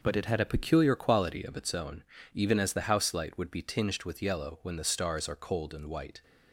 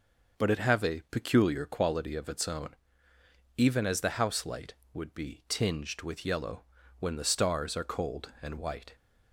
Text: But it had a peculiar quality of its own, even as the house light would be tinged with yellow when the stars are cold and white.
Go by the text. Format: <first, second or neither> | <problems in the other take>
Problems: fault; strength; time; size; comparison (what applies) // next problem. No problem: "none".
first | says "have" for "had"; at 0.5 s // pauses between "yellow" and "when"; slight; at 6.6 s; 0.36 s long